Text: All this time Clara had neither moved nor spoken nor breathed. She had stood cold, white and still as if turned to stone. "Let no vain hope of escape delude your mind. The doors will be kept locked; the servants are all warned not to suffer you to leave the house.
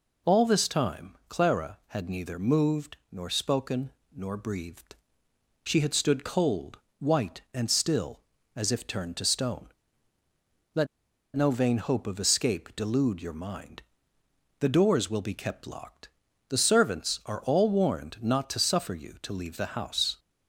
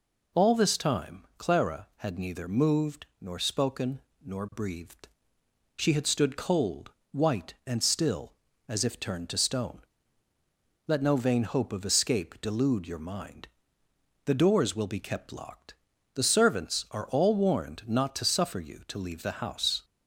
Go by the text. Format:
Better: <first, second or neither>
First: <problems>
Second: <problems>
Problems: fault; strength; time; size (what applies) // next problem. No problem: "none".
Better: second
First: pauses between "moved" and "nor"; slight; at 2.9 s; 0.16 s long // pauses between "spoken" and "nor"; slight; at 3.9 s; 0.24 s long // pauses between "Let" and "no"; noticeable; at 10.8 s; 0.47 s long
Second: pauses between "moved" and "nor"; slight; at 3.0 s; 0.16 s long // pauses between "spoken" and "nor"; slight; at 4.0 s; 0.24 s long